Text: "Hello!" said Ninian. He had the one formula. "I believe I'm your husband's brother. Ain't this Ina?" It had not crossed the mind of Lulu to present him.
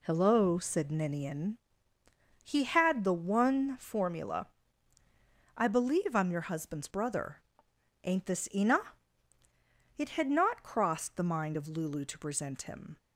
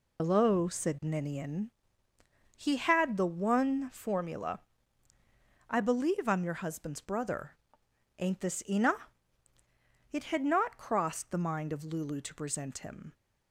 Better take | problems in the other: first | loses the start of "Hello"; at 0.1 s; 70 ms

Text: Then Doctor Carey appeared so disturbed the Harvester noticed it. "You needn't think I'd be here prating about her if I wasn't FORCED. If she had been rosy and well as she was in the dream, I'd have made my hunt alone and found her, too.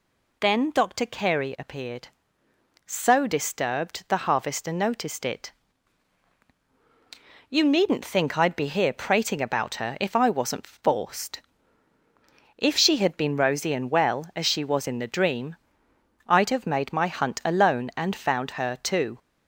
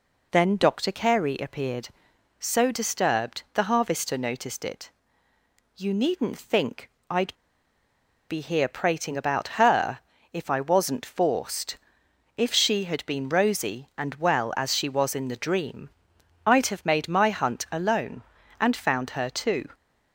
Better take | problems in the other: first | pauses between "think" and "I'd"; slight; at 6.8 s; 0.22 s long // pauses between "I'd" and "be"; noticeable; at 7.3 s; 0.95 s long // pauses between "her" and "if"; slight; at 9.9 s; 0.34 s long

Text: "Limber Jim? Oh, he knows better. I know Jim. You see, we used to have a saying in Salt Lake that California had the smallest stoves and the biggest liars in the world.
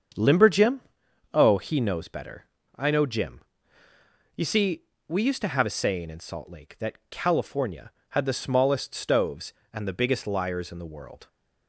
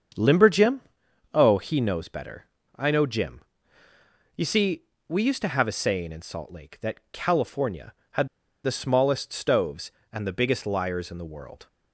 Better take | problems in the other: first | starts louder than the rest; until 1.6 s; 7 dB; also in the first // pauses between "had" and "the"; at 8.2 s; 0.37 s long

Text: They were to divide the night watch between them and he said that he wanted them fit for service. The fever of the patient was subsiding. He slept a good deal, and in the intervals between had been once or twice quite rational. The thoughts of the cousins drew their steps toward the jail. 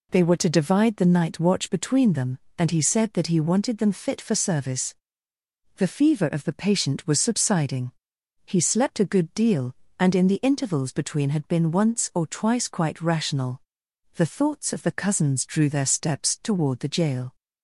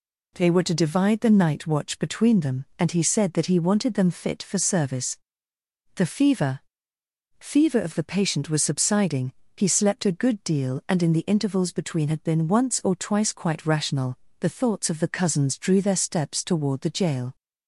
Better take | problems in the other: first | says "fever" twice; at 7.3 s

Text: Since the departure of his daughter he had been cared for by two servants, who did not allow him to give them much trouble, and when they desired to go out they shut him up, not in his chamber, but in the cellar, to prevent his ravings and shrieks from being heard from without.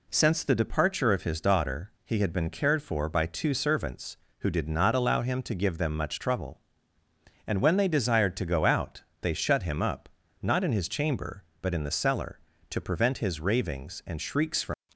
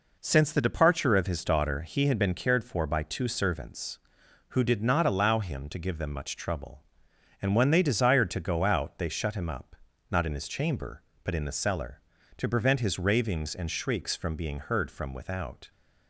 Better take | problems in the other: second | pauses between "out" and "they"; slight; at 9.0 s; 0.18 s long // stops before "being heard from without"; at 14.9 s

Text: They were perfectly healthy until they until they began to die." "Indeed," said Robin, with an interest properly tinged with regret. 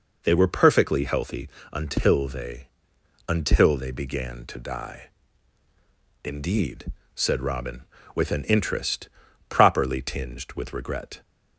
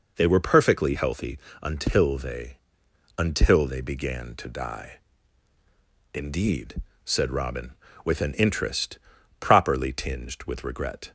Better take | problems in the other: neither | pauses between "healthy" and "until"; slight; the same in both // pauses between "they" and "until"; noticeable; the same in both // pauses between "interest" and "properly"; the same in both

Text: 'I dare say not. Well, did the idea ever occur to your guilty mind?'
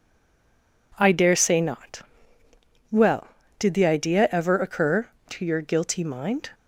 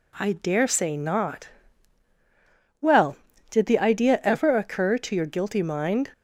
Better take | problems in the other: second | stays silent before the first word; slight; until 0.9 s; 0.9 s long

